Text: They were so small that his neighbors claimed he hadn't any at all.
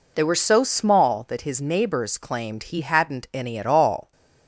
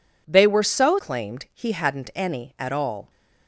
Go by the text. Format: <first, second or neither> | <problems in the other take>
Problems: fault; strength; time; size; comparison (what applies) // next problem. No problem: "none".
first | skips "small that his neighbors"; at 0.9 s